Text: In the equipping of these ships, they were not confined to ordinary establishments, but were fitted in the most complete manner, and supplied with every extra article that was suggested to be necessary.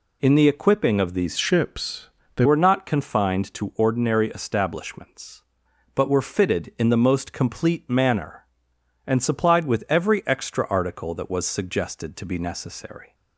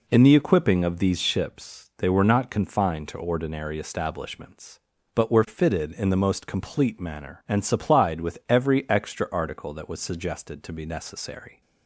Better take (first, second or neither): second